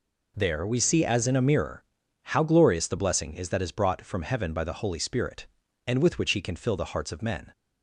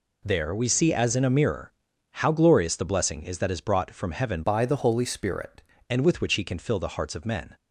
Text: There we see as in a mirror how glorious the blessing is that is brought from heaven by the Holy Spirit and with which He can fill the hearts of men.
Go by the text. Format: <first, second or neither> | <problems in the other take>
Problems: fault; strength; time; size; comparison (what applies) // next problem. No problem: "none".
first | pauses between "mirror" and "how"; at 1.7 s; 0.38 s long; also in the first // changes voice from "by" to "Spirit"; from 4.4 to 5.6 s; 1.2 s long